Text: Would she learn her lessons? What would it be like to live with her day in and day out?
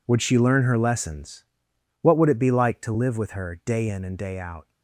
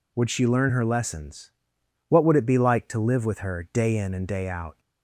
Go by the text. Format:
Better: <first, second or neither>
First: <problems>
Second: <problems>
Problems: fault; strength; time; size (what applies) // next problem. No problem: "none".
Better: second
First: gets quieter; strong; throughout; 14 dB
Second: none